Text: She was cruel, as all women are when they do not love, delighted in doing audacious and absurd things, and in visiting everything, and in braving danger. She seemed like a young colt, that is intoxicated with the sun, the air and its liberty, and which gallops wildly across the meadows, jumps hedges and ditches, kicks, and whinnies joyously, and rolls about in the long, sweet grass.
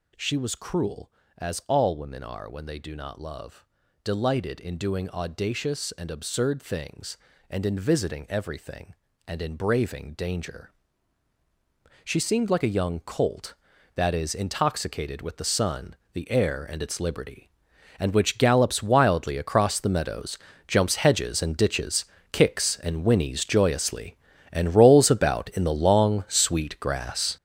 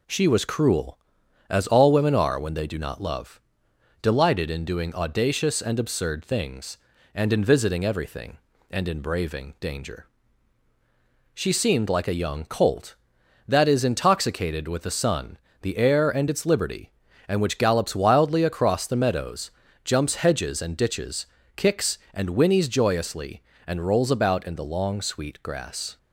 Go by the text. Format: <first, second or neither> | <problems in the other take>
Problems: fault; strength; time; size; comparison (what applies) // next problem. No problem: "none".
second | gets louder; strong; throughout; 9.5 dB